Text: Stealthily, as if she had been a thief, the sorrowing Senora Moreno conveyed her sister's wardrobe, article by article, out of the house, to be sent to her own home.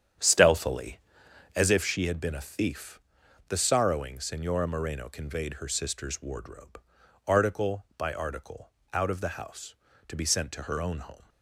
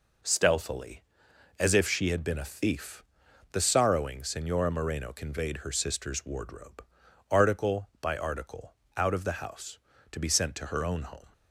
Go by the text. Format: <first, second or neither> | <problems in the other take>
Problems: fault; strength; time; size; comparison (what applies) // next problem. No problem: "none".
second | starts louder than the rest; strong; until 1.8 s; 9 dB